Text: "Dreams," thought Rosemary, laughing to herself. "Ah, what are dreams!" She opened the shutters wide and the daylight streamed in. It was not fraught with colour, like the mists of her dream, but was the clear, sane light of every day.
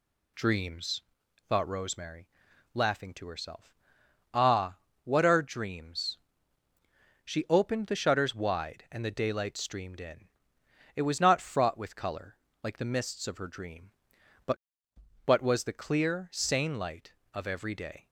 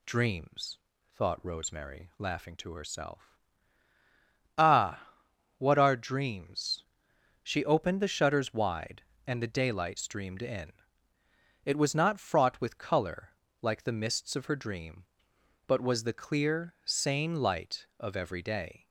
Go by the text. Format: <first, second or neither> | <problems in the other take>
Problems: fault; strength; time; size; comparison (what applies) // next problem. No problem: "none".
second | says "but" twice; at 15.2 s